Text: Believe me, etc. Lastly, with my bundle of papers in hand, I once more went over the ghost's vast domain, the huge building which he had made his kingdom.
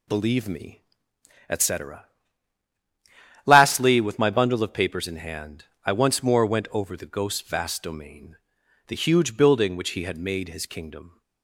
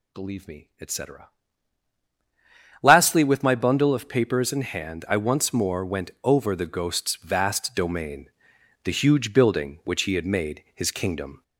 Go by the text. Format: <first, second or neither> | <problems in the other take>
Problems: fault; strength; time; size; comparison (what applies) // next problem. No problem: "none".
first | gets louder; slight; throughout; 2 dB